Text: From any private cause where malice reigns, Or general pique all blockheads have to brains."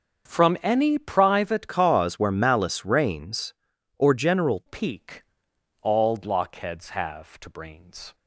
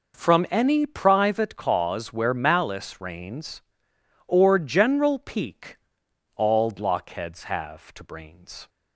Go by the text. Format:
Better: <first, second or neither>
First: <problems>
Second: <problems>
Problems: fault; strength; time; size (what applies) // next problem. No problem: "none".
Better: second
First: starts louder than the rest; until 1.3 s; 6.5 dB // changes voice from "cause" to "general"; from 1.6 to 4.6 s; 3.0 s long // pauses between "pique" and "all"; noticeable; at 5.2 s; 0.58 s long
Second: pauses between "pique" and "all"; noticeable; at 5.7 s; 0.58 s long